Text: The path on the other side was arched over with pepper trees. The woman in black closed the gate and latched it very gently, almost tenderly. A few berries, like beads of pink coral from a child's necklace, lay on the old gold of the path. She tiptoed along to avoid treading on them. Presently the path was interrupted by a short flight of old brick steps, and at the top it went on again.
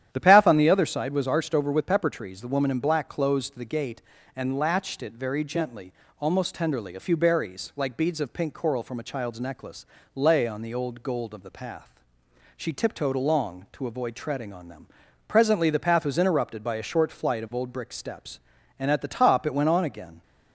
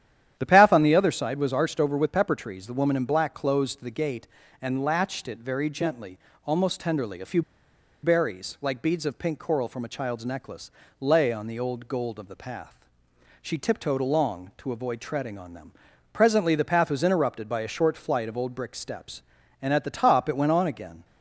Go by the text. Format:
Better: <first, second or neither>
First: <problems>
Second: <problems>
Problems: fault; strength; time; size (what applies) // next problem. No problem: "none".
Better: first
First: starts louder than the rest; strong; until 1.1 s; 10.5 dB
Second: starts louder than the rest; strong; until 1.3 s; 10.5 dB // pauses between "few" and "berries"; noticeable; at 7.4 s; 0.62 s long